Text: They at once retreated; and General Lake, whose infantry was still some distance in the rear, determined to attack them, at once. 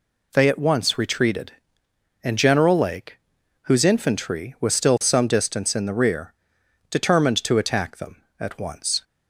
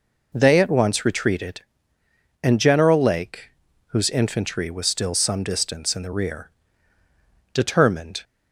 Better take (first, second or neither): first